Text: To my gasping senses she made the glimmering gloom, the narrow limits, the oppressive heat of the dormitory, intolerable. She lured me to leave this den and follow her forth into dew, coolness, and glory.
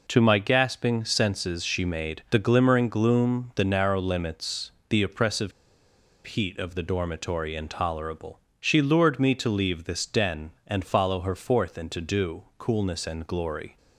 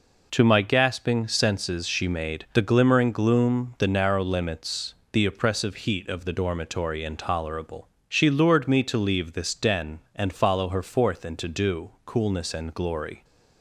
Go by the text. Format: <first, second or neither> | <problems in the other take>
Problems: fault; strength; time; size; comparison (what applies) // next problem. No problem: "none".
second | pauses between "oppressive" and "heat"; noticeable; at 5.5 s; 0.73 s long